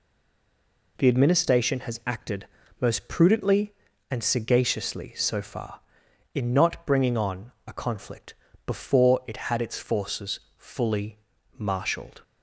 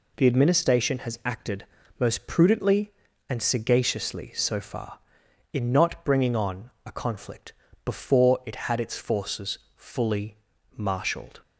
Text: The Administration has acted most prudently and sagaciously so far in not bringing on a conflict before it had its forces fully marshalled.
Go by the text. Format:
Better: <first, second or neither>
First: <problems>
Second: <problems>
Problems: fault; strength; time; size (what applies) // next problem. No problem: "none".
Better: second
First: stays silent before the first word; until 0.9 s; 0.9 s long // pauses between "acted" and "most"; slight; at 2.4 s; 0.34 s long // pauses between "on" and "a"; slight; at 7.5 s; 0.16 s long // pauses between "conflict" and "before"; slight; at 8.3 s; 0.32 s long // pauses between "forces" and "fully"; slight; at 10.3 s; 0.18 s long // pauses between "fully" and "marshalled"; at 11.1 s; 0.40 s long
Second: pauses between "acted" and "most"; slight; at 1.6 s; 0.34 s long // pauses between "on" and "a"; slight; at 6.7 s; 0.16 s long // pauses between "conflict" and "before"; slight; at 7.5 s; 0.32 s long // pauses between "forces" and "fully"; slight; at 9.5 s; 0.18 s long // pauses between "fully" and "marshalled"; at 10.3 s; 0.40 s long